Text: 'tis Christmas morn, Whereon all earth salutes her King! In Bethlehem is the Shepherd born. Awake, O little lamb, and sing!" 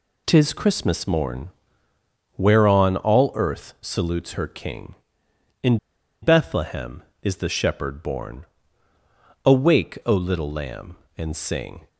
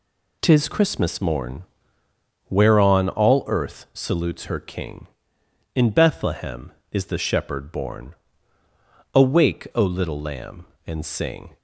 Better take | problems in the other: second | pauses between "In" and "Bethlehem"; at 5.7 s; 0.45 s long

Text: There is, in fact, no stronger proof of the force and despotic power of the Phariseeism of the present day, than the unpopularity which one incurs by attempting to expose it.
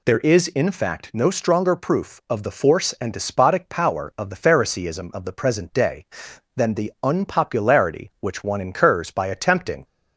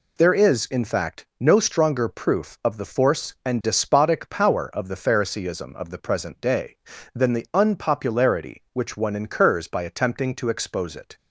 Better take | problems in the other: second | stops before "to expose it"; at 9.8 s

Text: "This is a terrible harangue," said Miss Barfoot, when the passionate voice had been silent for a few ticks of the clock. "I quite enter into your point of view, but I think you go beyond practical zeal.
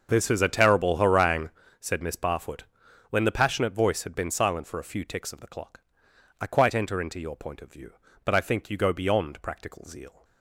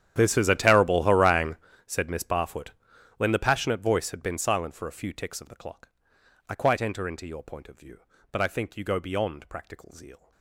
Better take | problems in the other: first | gets quieter; strong; throughout; 22 dB // starts louder than the rest; strong; until 1.1 s; 10.5 dB; also in the first

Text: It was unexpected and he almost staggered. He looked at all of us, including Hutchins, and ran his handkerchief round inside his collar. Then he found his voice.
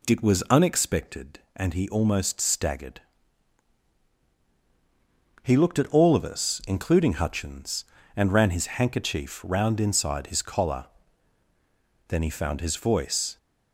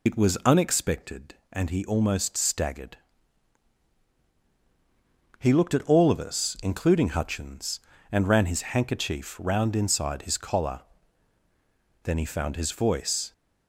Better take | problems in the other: first | loses the start of "It"; at 0.0 s; 75 ms

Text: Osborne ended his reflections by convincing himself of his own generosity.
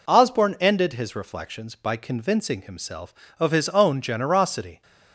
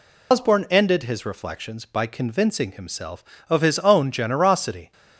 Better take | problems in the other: first | loses the start of "Osborne"; at 0.3 s; 130 ms

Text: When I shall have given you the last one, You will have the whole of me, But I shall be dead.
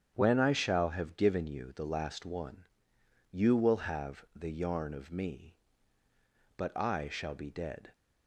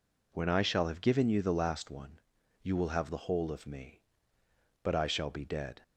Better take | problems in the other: second | starts louder than the rest; strong; until 1.1 s; 8.5 dB // says "yarn" for "whole"; at 4.5 s

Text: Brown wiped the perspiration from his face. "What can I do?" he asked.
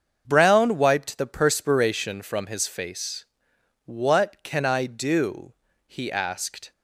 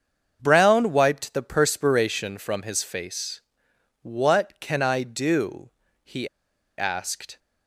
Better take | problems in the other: first | starts louder than the rest; until 1.4 s; 7 dB; also in the first // pauses between "he" and "asked"; noticeable; at 6.2 s; 0.51 s long

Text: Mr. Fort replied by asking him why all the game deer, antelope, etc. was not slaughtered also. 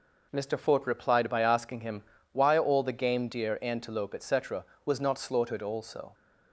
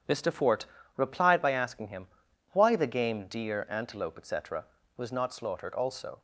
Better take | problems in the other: first | starts louder than the rest; strong; until 1.3 s; 9 dB // pauses between "Fort" and "replied"; slight; at 0.6 s; 0.32 s long // pauses between "him" and "why"; at 2.0 s; 0.44 s long; slight in the first // skips "all"; at 2.7 s

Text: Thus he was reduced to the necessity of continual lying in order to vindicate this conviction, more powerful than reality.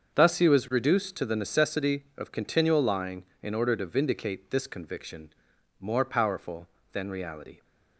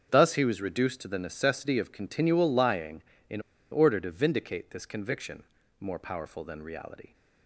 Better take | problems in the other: first | starts louder than the rest; until 1.1 s; 7 dB; also in the first // pauses between "in" and "order"; slight; at 3.3 s; 0.31 s long

